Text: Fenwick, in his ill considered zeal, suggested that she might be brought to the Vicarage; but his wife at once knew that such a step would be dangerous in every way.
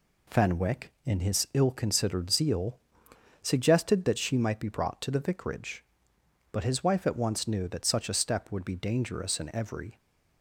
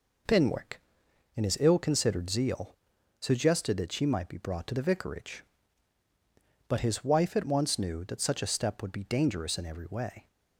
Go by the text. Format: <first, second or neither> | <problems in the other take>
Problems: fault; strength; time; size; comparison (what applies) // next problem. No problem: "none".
second | stops before "way"; at 9.9 s